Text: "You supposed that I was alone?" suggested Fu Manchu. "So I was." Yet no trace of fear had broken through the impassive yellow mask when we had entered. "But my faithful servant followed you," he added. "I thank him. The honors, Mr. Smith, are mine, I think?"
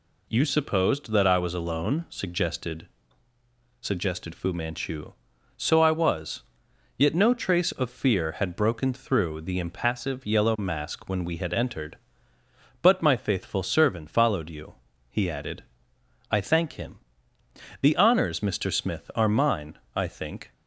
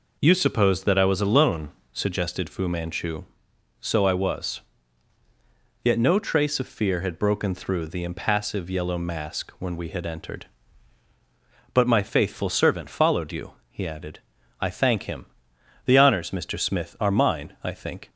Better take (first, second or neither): second